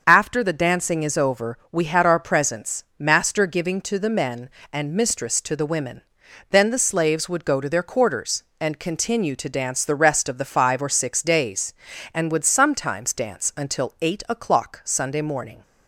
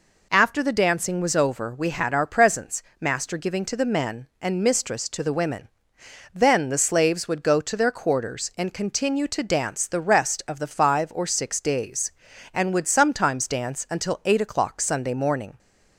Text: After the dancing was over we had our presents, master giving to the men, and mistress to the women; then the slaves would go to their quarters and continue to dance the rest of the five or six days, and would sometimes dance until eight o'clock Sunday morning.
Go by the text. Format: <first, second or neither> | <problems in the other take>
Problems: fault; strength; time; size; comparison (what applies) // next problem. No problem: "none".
second | starts louder than the rest; until 1.0 s; 6.5 dB // says "is" for "was"; at 1.0 s